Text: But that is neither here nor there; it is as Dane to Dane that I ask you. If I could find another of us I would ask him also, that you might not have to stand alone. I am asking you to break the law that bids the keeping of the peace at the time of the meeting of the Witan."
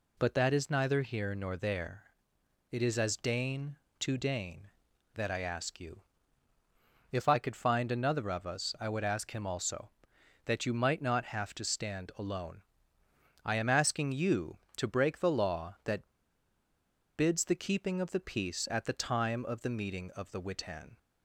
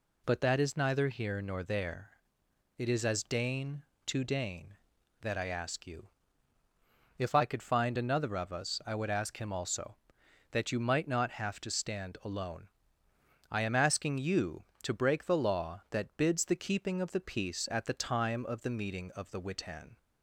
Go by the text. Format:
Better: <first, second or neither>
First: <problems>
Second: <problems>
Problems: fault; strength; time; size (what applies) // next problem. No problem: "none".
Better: second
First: pauses between "that" and "bids"; at 16.1 s; 1.0 s long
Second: none